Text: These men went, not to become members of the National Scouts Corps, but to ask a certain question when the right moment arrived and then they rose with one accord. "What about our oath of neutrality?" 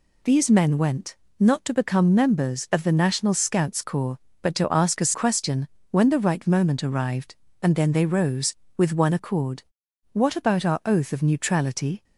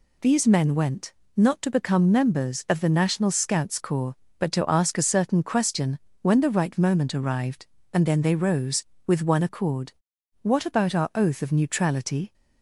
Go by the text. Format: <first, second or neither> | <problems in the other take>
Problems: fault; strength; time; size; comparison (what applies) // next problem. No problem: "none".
second | skips "certain"; at 5.1 s // pauses between "question" and "when"; slight; at 5.6 s; 0.24 s long; slight in the second